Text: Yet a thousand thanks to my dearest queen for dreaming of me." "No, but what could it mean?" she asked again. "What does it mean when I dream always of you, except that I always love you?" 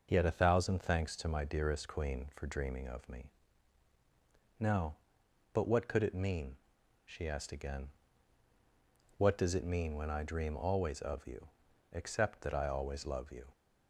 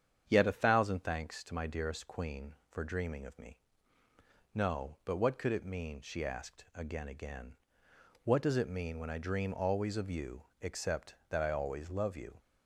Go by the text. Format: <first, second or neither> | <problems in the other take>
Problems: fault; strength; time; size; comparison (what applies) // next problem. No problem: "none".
first | starts louder than the rest; strong; until 1.2 s; 8 dB // says "again" twice; at 7.0 s